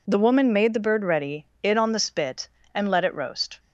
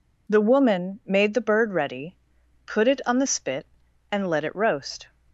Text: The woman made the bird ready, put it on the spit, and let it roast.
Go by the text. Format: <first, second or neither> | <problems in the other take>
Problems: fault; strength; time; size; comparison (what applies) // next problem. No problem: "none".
second | skips "put"; at 1.5 s